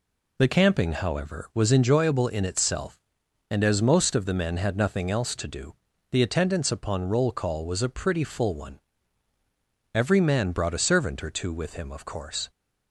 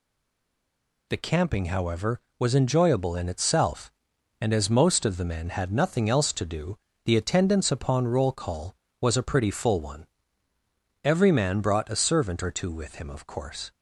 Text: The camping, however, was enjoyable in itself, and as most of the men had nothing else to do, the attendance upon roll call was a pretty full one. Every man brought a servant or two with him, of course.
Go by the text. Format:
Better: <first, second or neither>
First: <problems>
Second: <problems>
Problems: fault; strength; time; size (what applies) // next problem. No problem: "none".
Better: first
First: none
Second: stays silent before the first word; until 1.0 s; 1.0 s long